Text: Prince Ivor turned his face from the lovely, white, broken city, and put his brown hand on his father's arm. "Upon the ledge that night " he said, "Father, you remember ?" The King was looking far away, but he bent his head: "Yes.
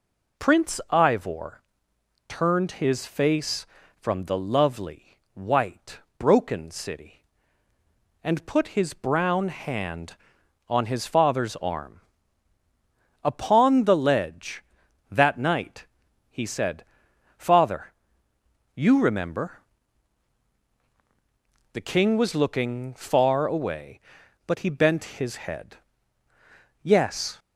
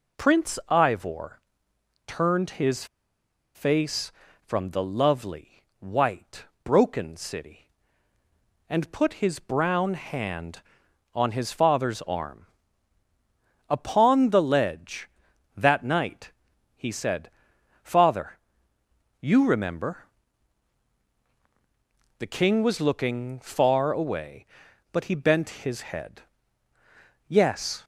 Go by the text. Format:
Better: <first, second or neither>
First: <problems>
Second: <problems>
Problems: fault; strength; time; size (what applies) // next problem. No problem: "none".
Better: first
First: pauses between "Ivor" and "turned"; noticeable; at 1.6 s; 0.66 s long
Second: pauses between "Ivor" and "turned"; noticeable; at 1.4 s; 0.66 s long // pauses between "his" and "face"; noticeable; at 2.8 s; 0.70 s long